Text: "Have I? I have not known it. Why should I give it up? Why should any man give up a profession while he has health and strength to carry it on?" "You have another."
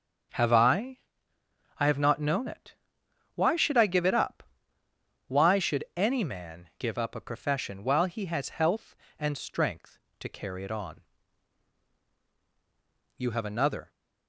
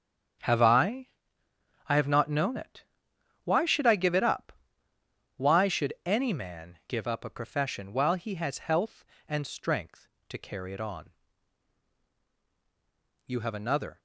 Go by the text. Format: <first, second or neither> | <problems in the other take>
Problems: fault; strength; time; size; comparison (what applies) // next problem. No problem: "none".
first | gets quieter; strong; throughout; 12.5 dB // starts louder than the rest; strong; until 2.2 s; 8.5 dB; strong in the first